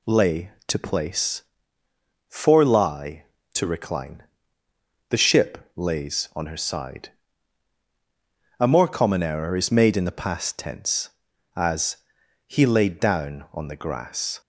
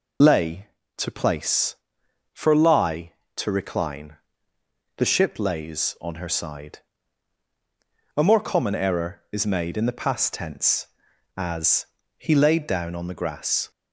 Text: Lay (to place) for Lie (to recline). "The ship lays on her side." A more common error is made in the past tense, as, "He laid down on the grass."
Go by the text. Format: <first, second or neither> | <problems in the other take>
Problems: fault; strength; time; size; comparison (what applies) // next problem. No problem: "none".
first | loses the start of "Lay"; at 0.2 s; 40 ms